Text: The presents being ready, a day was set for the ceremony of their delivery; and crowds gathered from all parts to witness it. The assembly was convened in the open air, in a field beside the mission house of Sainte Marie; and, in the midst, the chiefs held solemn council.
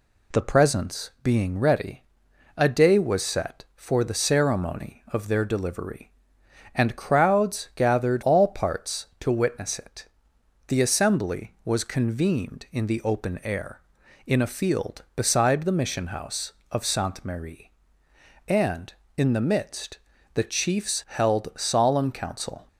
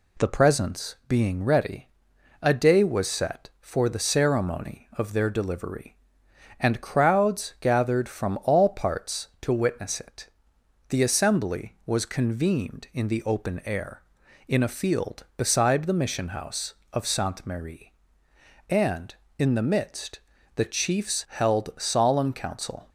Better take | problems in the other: second | skips "from"; at 8.2 s

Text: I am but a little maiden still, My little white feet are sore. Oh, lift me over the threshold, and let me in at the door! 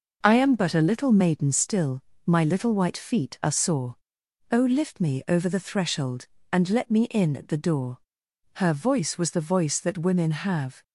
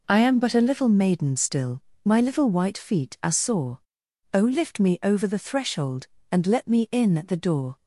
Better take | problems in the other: second | goes on to say "Her voice was the voice that women have"; strong; from 8.5 s on; 2.2 s long

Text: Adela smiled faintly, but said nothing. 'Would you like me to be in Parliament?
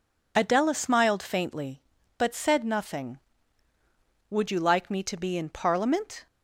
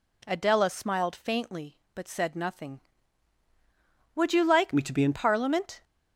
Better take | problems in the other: first | changes voice from "me" to "in"; from 4.7 to 5.1 s; 0.4 s long

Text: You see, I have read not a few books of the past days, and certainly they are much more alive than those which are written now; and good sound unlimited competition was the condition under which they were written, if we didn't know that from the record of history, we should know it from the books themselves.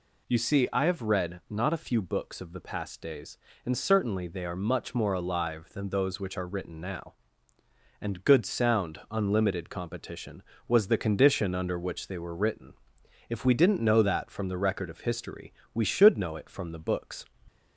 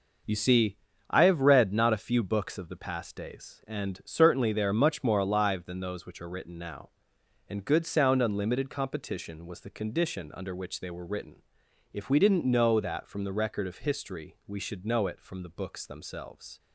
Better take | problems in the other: second | stops before "themselves"; at 17.4 s

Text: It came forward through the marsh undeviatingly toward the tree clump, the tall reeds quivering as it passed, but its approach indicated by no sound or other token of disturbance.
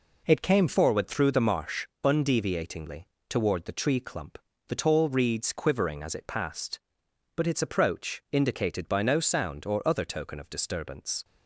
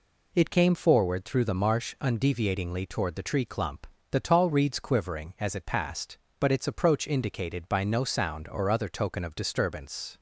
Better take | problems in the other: second | changes voice at "forward"; from 0.6 s on; 10.6 s long // pauses between "marsh" and "undeviatingly"; slight; at 1.8 s; 0.18 s long // pauses between "undeviatingly" and "toward"; slight; at 3.0 s; 0.22 s long

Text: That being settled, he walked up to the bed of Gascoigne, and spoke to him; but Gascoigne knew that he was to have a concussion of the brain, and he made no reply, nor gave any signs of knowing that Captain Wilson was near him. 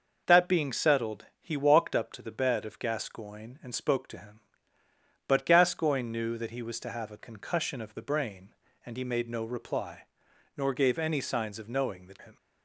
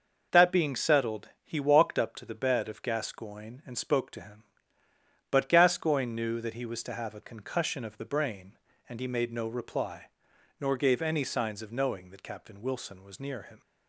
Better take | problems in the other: second | skips "Captain Wilson was near"; at 12.1 s

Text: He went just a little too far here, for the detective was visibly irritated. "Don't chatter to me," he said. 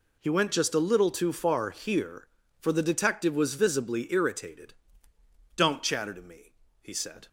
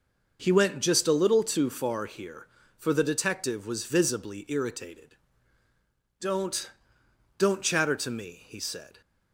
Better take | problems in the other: first | says "Don't" twice; at 7.3 s

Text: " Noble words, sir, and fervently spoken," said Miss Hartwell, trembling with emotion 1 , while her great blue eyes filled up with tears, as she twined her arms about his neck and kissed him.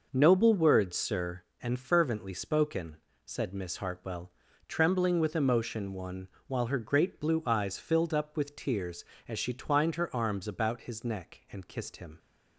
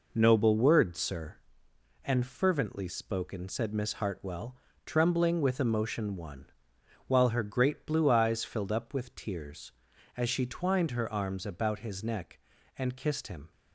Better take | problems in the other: neither | none

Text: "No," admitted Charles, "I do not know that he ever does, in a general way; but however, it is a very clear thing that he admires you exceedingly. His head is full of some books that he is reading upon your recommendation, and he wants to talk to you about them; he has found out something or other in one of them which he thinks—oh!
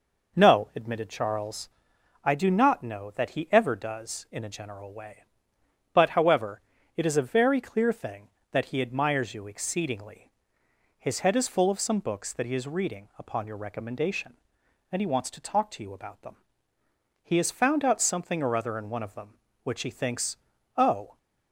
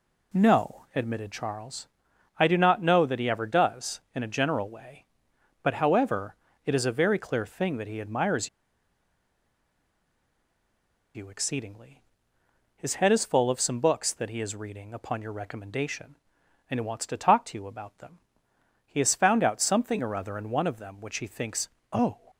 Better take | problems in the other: first | pauses between "admires" and "you"; strong; at 8.4 s; 2.6 s long

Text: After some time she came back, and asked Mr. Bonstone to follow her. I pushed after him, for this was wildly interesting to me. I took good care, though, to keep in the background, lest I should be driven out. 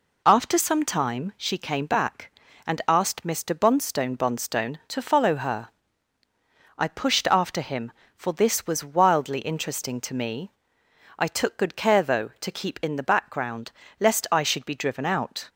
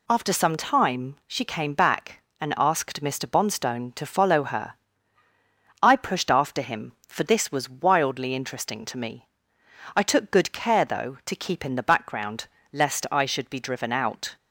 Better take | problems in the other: second | says "Bonstone" twice; at 4.1 s

